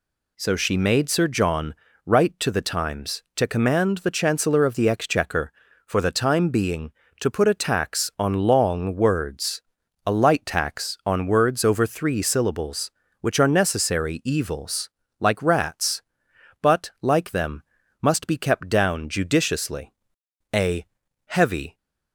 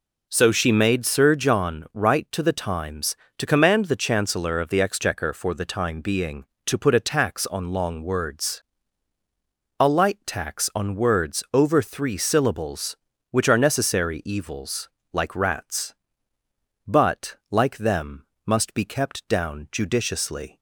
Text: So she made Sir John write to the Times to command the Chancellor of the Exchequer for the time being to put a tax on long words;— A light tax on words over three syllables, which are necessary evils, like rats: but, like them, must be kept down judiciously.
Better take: second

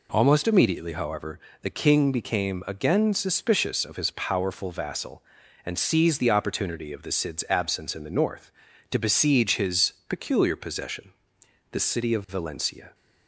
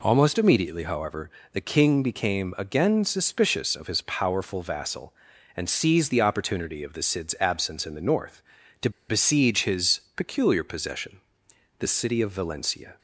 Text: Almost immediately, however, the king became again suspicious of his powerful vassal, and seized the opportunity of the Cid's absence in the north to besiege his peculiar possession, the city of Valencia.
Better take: first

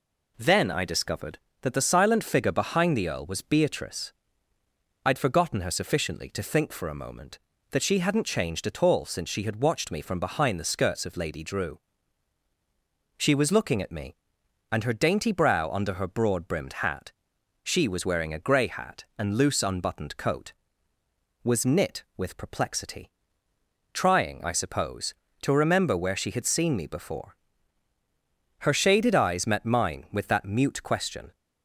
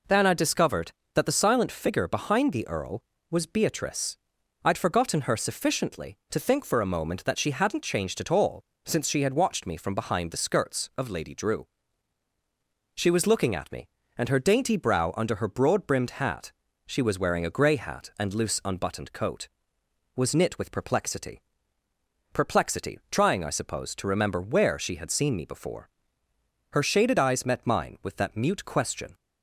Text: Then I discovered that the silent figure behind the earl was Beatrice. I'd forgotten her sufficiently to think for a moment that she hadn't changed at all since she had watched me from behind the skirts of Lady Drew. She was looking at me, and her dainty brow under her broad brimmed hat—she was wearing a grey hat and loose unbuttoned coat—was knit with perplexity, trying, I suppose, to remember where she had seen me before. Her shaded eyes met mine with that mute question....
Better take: first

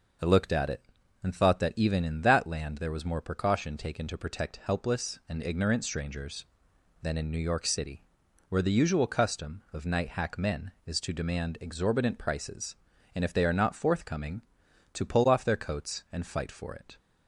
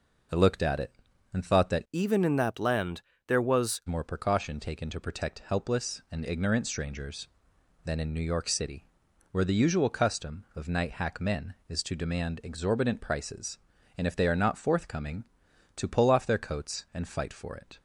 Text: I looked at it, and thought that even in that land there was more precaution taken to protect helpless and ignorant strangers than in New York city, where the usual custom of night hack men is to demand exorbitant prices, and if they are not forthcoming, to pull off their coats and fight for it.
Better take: first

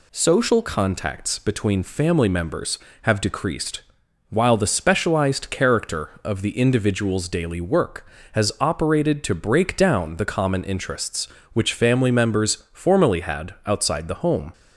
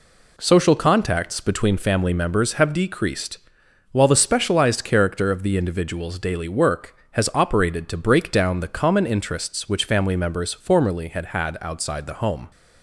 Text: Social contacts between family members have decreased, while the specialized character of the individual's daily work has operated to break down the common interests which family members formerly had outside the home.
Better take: first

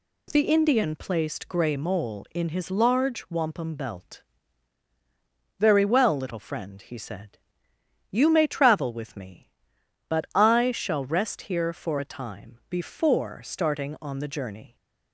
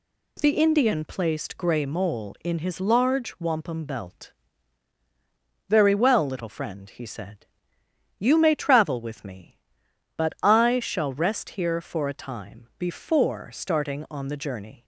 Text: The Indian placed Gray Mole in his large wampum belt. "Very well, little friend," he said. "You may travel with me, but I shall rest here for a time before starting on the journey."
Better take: neither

